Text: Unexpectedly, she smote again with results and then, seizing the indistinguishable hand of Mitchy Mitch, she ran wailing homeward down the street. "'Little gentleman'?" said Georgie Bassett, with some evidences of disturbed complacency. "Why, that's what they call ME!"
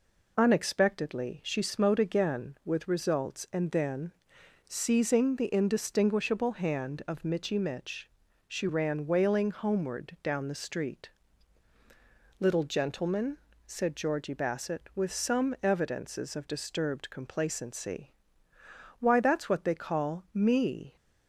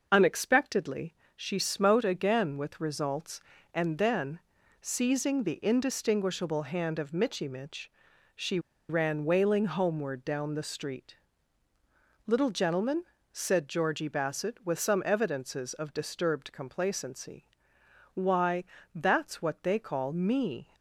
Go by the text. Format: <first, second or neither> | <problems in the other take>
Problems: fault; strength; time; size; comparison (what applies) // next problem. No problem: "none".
first | pauses between "she" and "ran"; slight; at 8.5 s; 0.30 s long